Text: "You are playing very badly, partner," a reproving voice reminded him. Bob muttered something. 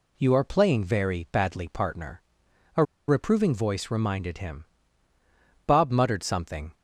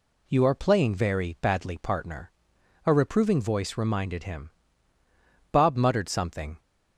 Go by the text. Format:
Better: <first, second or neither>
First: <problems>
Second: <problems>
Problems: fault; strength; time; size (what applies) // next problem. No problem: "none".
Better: second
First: pauses between "a" and "reproving"; slight; at 2.8 s; 0.25 s long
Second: none